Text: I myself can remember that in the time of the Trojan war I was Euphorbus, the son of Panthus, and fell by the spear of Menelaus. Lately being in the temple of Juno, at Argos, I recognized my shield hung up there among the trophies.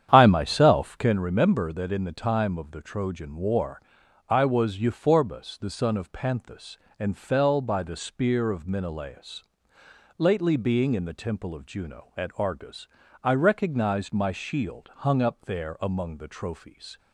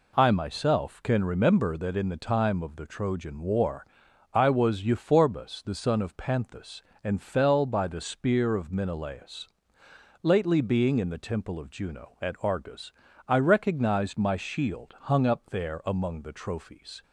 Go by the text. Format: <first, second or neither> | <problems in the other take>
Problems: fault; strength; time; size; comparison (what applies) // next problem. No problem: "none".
second | starts louder than the rest; strong; until 1.2 s; 9.5 dB // pauses between "war" and "I"; noticeable; at 3.7 s; 0.48 s long; noticeable in the second